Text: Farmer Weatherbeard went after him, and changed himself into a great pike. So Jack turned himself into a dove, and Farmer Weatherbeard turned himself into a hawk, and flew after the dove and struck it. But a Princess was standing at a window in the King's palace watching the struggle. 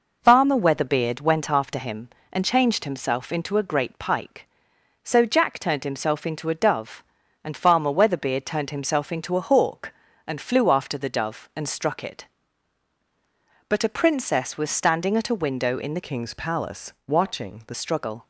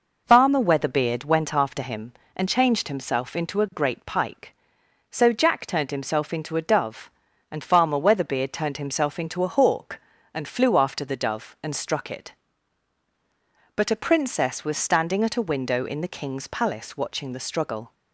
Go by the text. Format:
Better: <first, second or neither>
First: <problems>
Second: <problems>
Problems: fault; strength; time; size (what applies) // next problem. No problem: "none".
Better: second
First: changes voice from "King's" to "the"; from 16.0 to 17.7 s; 1.7 s long // pauses between "palace" and "watching"; slight; at 16.9 s; 0.16 s long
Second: none